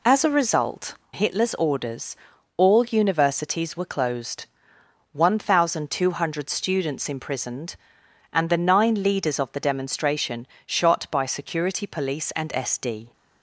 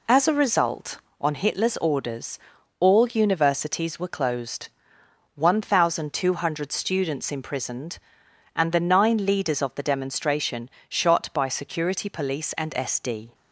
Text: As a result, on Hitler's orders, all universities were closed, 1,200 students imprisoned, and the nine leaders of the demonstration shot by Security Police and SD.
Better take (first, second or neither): second